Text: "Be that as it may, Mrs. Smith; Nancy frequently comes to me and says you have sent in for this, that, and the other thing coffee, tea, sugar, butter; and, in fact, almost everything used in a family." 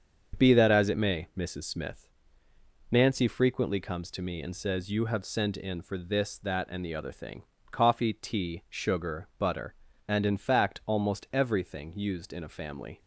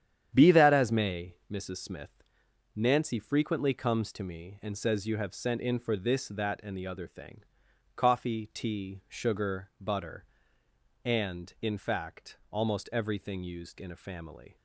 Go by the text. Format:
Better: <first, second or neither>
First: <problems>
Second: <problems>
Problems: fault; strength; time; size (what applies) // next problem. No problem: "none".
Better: first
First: starts louder than the rest; until 1.4 s; 7 dB // pauses between "thing" and "coffee"; slight; at 7.4 s; 0.26 s long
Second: starts louder than the rest; strong; until 1.3 s; 9.5 dB // skips "it"; at 0.9 s // pauses between "thing" and "coffee"; noticeable; at 7.4 s; 0.52 s long